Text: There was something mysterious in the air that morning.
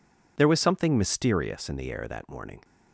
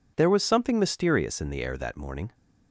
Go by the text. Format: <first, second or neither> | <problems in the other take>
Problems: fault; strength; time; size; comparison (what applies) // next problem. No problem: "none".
neither | none